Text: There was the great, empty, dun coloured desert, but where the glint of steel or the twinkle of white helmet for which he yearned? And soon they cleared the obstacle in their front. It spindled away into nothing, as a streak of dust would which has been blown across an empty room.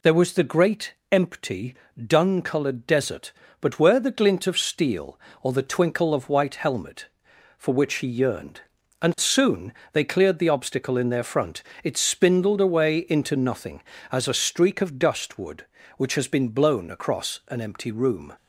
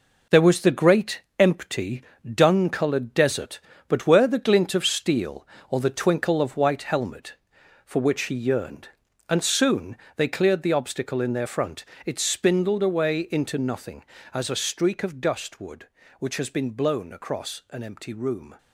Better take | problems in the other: first | gets quieter; strong; throughout; 7.5 dB // pauses between "soon" and "they"; slight; at 9.9 s; 0.20 s long; slight in the first

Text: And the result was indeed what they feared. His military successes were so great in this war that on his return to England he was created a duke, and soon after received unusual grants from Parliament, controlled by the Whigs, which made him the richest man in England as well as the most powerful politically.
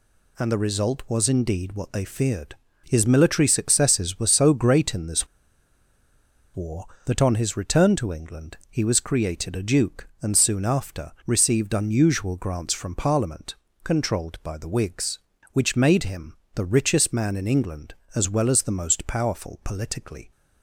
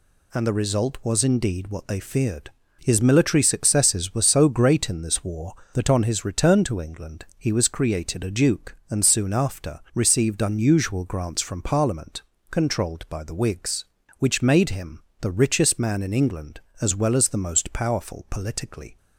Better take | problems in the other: second | pauses between "this" and "war"; strong; at 5.2 s; 1.2 s long // pauses between "him" and "the"; slight; at 16.3 s; 0.18 s long; slight in the second

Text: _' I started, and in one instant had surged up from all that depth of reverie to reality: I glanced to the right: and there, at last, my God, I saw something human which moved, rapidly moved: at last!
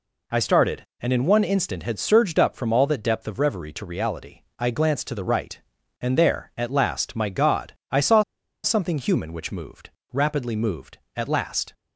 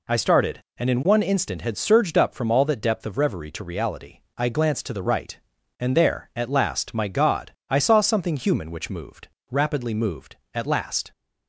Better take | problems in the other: second | pauses between "saw" and "something"; at 8.2 s; 0.41 s long

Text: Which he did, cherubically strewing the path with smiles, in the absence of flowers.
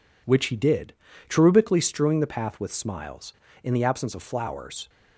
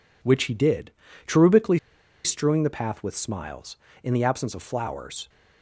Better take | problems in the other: first | pauses between "cherubically" and "strewing"; at 1.7 s; 0.45 s long

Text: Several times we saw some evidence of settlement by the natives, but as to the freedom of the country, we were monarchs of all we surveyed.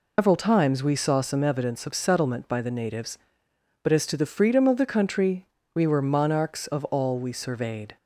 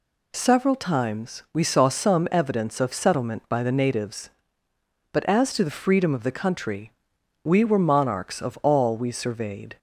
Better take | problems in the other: second | loses the start of "Several"; at 0.1 s; 165 ms

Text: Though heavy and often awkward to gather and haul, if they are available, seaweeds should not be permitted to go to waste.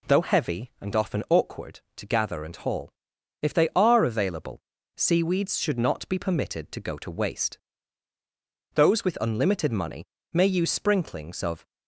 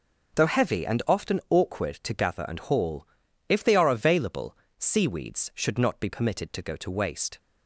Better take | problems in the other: second | goes on to say "Those with unlimited money may use sprinklings of"; strong; from 8.7 s on; 2.9 s long

